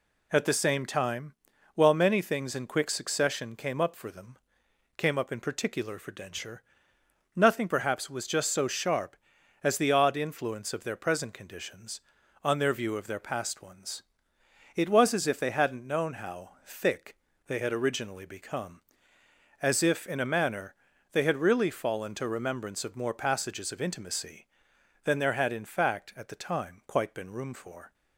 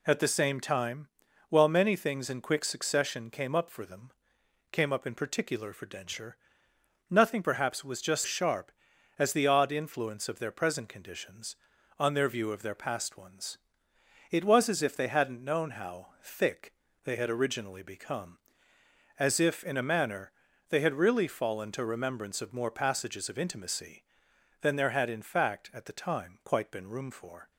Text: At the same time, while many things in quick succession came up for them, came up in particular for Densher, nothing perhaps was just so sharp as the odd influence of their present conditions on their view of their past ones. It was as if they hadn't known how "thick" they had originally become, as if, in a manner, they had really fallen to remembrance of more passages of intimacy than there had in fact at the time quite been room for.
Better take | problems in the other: first | skips "so"; at 8.2 s // pauses between "thick" and "they"; slight; at 16.7 s; 0.32 s long; slight in the first

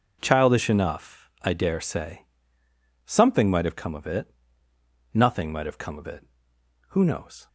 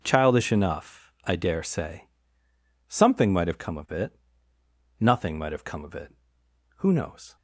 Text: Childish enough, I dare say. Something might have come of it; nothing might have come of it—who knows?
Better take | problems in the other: neither | none

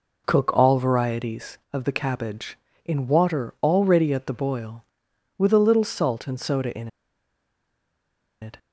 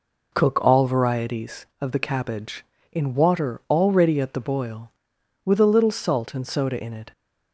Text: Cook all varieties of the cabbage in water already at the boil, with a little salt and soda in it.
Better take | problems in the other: second | pauses between "in" and "it"; strong; at 6.8 s; 1.5 s long

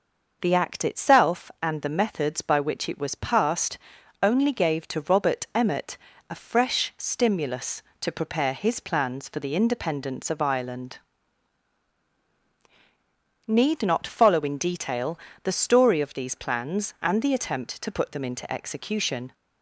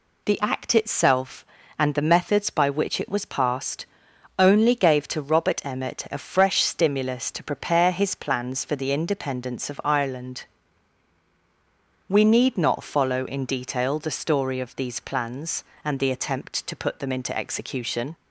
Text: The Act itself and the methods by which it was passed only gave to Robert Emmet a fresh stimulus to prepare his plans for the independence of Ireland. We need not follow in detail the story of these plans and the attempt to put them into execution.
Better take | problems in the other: second | pauses between "passed" and "only"; noticeable; at 3.7 s; 0.46 s long; noticeable in the second // pauses between "Emmet" and "a"; slight; at 5.9 s; 0.32 s long // skips "We"; at 12.2 s // pauses between "detail" and "the"; slight; at 15.1 s; 0.24 s long

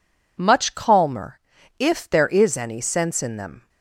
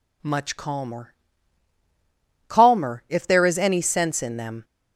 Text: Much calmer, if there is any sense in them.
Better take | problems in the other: first | says "calmer" twice; at 2.4 s

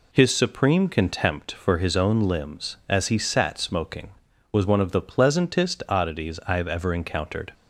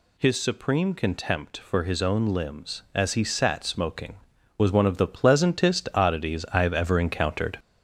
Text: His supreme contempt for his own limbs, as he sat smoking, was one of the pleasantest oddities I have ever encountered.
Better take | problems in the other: first | gets louder; noticeable; throughout; 5 dB

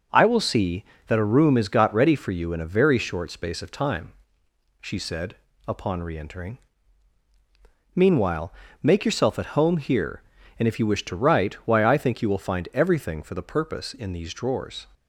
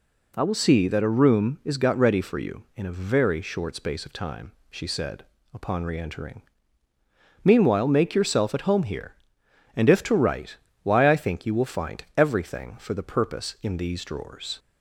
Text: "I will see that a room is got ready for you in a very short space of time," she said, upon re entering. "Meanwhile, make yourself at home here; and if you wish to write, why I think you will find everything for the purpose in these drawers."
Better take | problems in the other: first | skips "you wish"; at 10.0 s

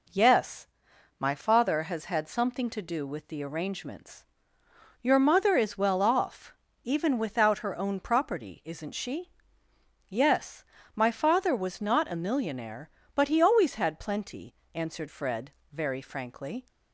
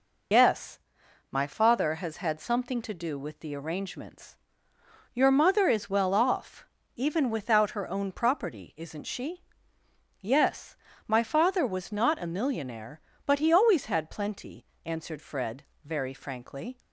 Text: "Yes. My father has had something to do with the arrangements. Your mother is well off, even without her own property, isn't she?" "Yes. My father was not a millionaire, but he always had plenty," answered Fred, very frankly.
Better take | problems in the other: first | loses the start of "Yes"; at 0.3 s; 115 ms

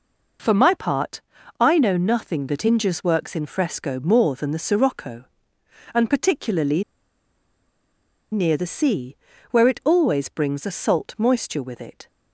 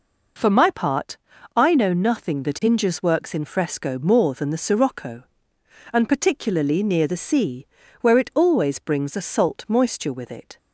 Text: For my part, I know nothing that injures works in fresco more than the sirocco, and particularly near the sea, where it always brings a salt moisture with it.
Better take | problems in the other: second | pauses between "particularly" and "near"; strong; at 6.8 s; 1.4 s long

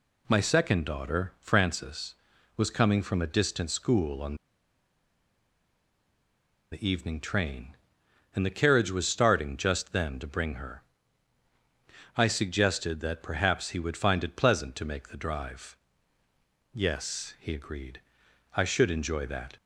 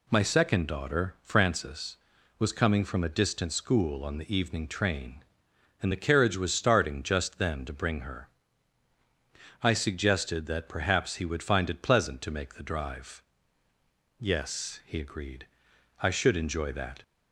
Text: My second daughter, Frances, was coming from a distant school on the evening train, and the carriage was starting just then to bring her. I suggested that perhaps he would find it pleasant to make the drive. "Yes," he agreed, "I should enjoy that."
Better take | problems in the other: second | pauses between "on" and "the"; strong; at 4.3 s; 2.3 s long

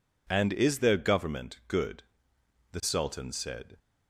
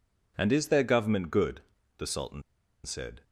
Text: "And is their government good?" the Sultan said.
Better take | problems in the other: first | pauses between "Sultan" and "said"; at 2.4 s; 0.42 s long

